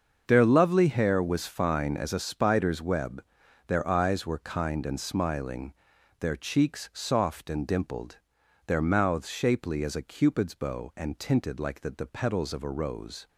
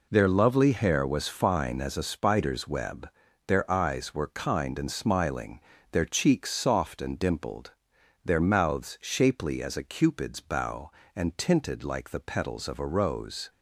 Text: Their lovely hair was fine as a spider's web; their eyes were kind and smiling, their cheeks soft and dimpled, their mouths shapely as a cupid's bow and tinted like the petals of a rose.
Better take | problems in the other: second | starts louder than the rest; until 1.2 s; 6.5 dB // says "the" twice; at 11.9 s

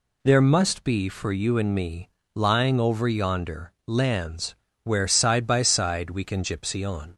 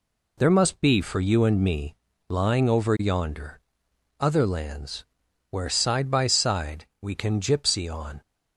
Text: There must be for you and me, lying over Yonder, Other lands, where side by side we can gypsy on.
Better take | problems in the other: second | skips "Other"; at 3.7 s

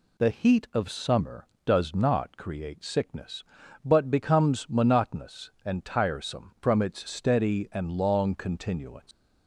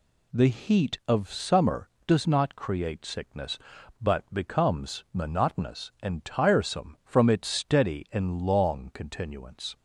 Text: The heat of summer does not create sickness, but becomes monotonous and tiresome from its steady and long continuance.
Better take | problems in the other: second | leaves "continuance" unfinished; at 9.1 s; 90 ms

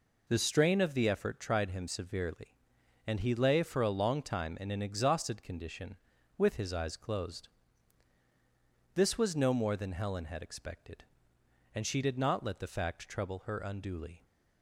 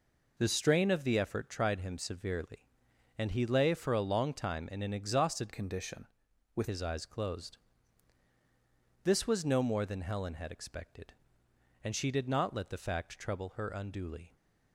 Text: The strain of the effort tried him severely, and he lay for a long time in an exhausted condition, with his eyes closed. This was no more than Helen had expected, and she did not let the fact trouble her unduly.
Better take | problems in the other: first | changes voice from "condition" to "with"; from 5.5 to 6.6 s; 1.1 s long

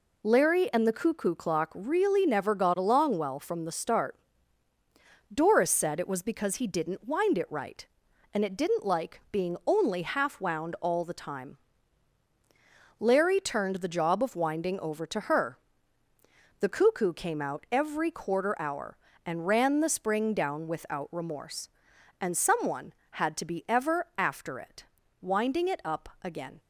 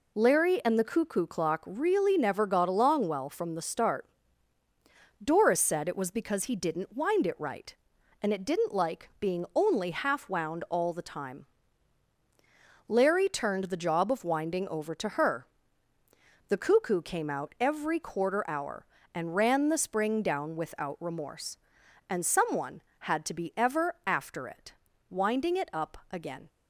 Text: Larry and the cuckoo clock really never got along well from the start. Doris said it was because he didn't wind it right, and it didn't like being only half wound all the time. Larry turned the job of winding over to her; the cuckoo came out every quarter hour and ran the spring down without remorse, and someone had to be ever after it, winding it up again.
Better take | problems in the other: neither | none

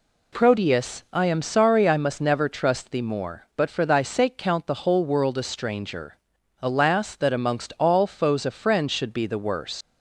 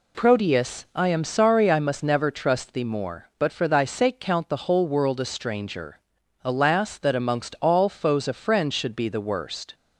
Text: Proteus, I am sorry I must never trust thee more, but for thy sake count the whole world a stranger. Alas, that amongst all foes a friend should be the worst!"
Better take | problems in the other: second | leaves "worst" unfinished; at 9.8 s; 105 ms

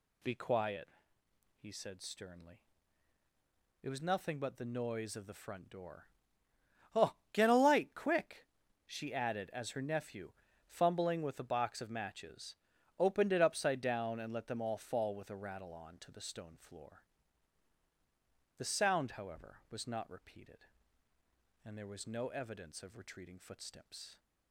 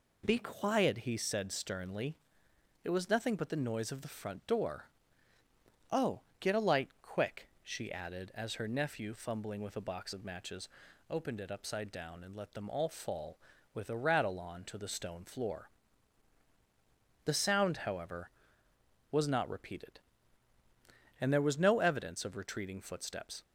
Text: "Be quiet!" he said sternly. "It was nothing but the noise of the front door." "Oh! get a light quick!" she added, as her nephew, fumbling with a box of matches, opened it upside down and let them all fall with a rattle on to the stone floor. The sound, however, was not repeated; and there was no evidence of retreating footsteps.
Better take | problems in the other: neither | none

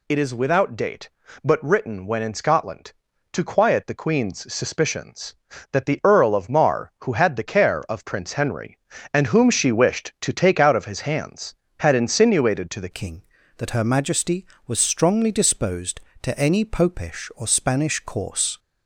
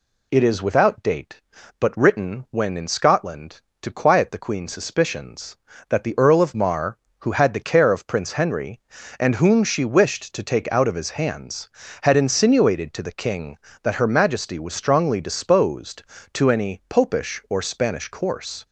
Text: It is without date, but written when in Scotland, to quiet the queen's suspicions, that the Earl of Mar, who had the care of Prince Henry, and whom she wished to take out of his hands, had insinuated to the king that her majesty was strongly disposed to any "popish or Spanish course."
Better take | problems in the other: second | changes voice at "king"; from 12.9 s on; 5.6 s long

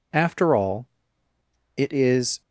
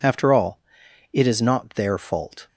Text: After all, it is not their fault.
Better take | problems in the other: second | stops before "not their fault"; at 2.4 s

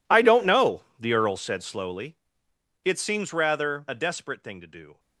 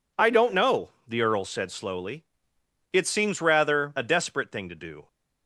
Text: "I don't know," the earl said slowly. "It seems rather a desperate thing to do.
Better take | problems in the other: second | gets quieter; strong; throughout; 21 dB

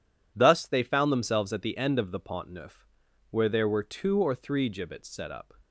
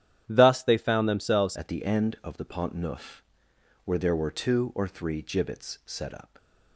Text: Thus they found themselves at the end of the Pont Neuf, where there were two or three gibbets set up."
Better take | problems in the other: first | starts louder than the rest; strong; until 1.2 s; 10.5 dB // changes voice at "at"; from 1.5 s on; 4.8 s long

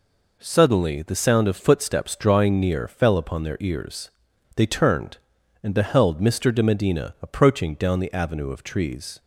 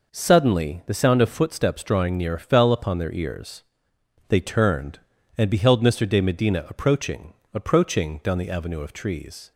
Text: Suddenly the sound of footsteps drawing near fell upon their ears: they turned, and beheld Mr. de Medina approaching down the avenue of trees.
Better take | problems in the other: first | says "approaching" twice; at 7.5 s

